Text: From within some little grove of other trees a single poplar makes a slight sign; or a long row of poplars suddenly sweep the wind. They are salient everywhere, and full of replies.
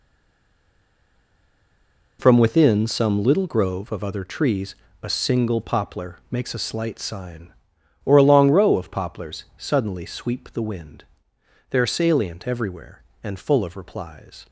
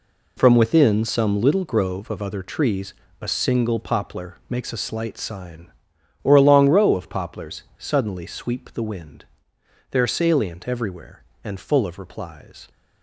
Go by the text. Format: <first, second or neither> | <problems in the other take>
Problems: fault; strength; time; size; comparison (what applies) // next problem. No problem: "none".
second | stays silent before the first word; until 2.1 s; 2.1 s long // pauses between "trees" and "a"; slight; at 4.7 s; 0.26 s long; slight in the second